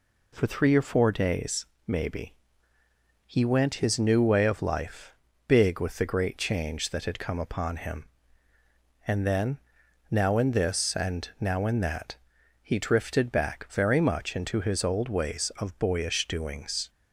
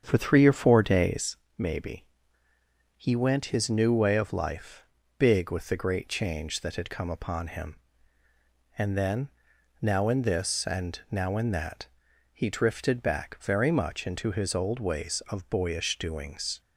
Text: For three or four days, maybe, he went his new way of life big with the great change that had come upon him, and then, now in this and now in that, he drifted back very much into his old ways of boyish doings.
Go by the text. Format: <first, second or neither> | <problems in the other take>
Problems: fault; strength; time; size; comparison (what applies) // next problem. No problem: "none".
first | starts louder than the rest; strong; until 1.3 s; 7.5 dB // pauses between "life" and "big"; slight; at 4.8 s; 0.32 s long; slight in the first